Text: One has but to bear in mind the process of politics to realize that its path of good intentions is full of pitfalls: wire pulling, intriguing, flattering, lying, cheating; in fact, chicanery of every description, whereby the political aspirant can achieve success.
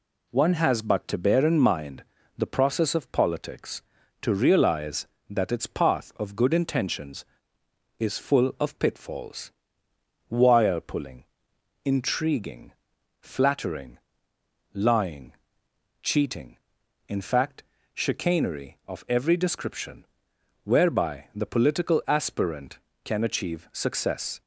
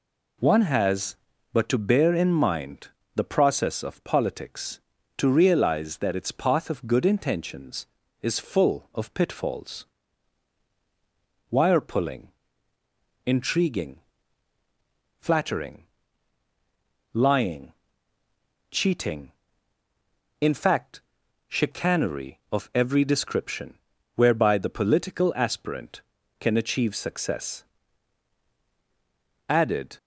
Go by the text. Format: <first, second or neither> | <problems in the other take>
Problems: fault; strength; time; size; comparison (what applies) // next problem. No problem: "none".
first | pauses between "mind" and "the"; slight; at 2.8 s; 0.26 s long; slight in the first // goes on to say "Added"; slight; from 29.4 s on; 0.48 s long